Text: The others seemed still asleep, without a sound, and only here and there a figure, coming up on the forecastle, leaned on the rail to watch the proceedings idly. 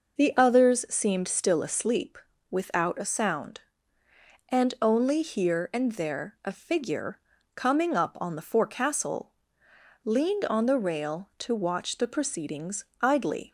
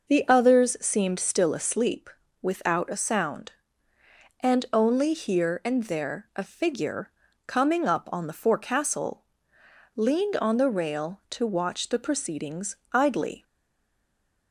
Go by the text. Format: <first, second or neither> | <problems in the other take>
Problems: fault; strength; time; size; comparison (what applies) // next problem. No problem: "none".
first | pauses between "proceedings" and "idly"; slight; at 12.7 s; 0.16 s long; slight in the first // stays silent after the last word; from 13.4 s on; 1.1 s long